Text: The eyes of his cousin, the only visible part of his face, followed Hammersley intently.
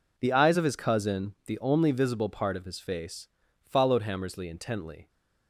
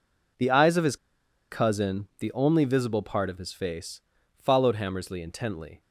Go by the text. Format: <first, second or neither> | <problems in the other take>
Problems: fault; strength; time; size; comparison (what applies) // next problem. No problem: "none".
first | pauses between "his" and "cousin"; noticeable; at 0.9 s; 0.54 s long